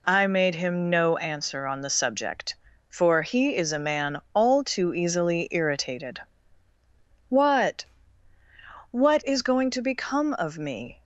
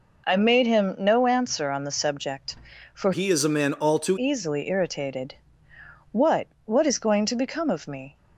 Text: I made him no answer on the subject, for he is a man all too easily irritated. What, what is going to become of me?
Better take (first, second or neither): first